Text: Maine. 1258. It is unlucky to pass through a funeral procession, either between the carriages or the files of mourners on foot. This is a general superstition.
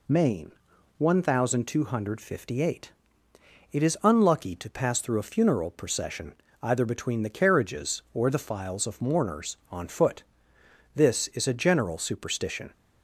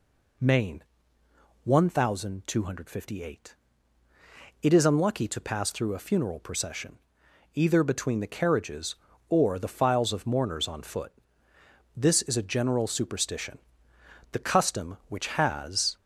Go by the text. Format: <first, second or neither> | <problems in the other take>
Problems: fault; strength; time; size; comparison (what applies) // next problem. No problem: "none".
first | goes on to say "The custom which has"; from 14.3 s on; 1.6 s long